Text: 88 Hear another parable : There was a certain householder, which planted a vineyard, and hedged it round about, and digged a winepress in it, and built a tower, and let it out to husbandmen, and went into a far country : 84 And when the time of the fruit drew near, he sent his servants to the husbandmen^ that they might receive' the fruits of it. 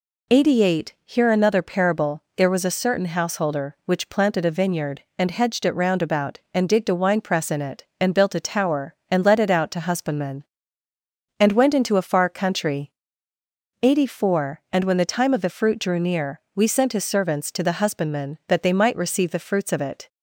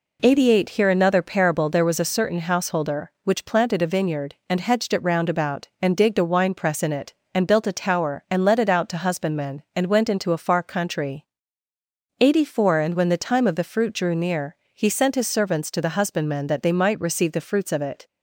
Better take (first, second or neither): second